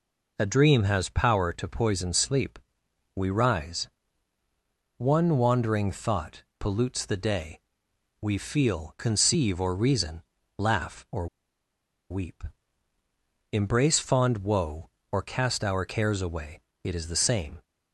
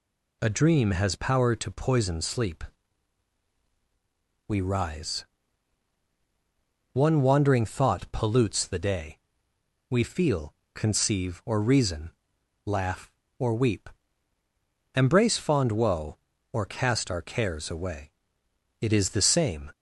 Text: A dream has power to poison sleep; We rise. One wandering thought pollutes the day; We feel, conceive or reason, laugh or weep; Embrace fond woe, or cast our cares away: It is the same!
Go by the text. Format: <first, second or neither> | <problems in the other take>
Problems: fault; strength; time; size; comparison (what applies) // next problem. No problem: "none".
second | pauses between "thought" and "pollutes"; slight; at 6.4 s; 0.16 s long // pauses between "or" and "weep"; noticeable; at 11.2 s; 0.84 s long